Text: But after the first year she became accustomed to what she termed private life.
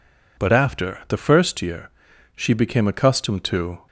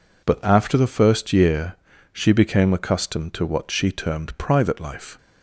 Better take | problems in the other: second | pauses between "year" and "she"; noticeable; at 1.8 s; 0.48 s long; also in the second // stops before "what she termed private life"; at 3.8 s

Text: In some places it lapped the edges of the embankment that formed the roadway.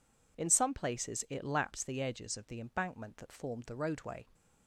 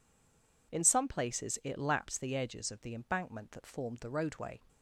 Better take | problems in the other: first | stays silent before the first word; slight; until 0.7 s; 0.7 s long

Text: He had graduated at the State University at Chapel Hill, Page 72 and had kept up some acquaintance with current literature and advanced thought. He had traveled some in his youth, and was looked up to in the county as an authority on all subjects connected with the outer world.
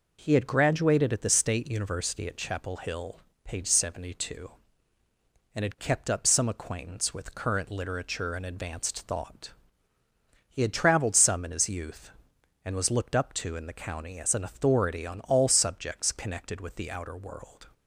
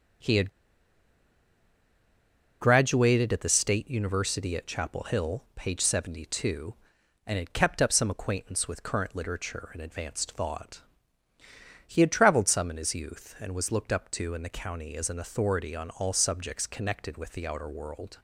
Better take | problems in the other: first | starts louder than the rest; until 3.3 s; 6.5 dB // pauses between "had" and "graduated"; strong; at 0.4 s; 2.1 s long

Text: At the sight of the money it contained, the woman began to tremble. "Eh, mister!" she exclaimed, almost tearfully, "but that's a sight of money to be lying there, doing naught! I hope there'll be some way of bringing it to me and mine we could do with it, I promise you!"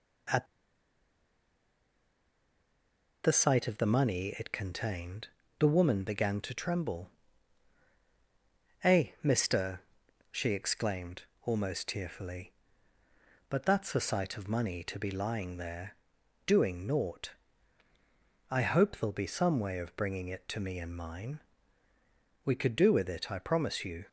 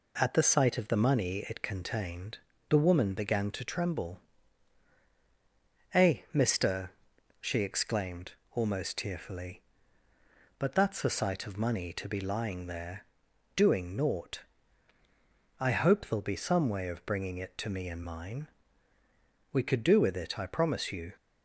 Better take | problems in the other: second | pauses between "At" and "the"; strong; at 0.4 s; 2.7 s long // pauses between "mine" and "we"; at 21.3 s; 1.0 s long; also in the second

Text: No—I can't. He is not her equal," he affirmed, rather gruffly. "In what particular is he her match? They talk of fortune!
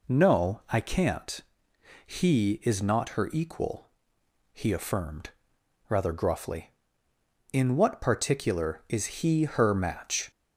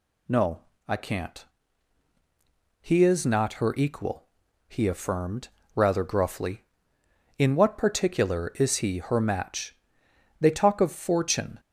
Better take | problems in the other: second | stops before "They talk of fortune"; at 10.3 s

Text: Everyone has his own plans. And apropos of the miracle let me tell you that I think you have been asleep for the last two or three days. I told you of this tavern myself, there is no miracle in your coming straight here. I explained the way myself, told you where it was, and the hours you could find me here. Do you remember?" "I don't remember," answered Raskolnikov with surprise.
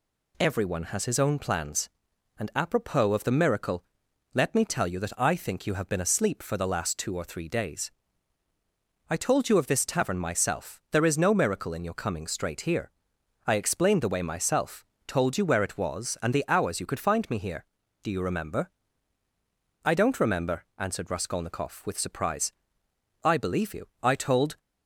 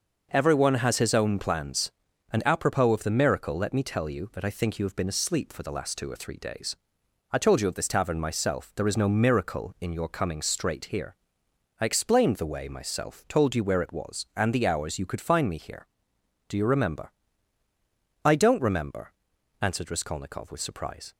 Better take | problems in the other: second | pauses between "miracle" and "let"; noticeable; at 3.8 s; 0.50 s long // goes on to say "I believe you I told"; from 23.2 s on; 1.3 s long

